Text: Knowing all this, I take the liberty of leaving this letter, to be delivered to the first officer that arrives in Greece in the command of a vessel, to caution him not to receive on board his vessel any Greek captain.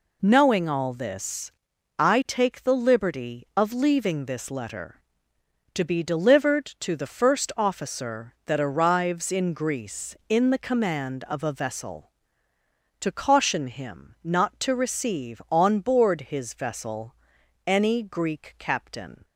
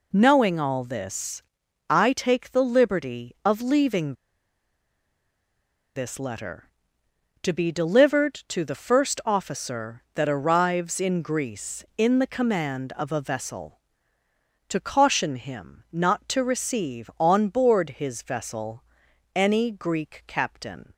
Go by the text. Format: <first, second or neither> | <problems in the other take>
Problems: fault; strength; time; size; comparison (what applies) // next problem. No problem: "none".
first | pauses between "leaving" and "this"; strong; at 4.1 s; 1.8 s long // pauses between "vessel" and "any"; noticeable; at 18.8 s; 0.50 s long; noticeable in the first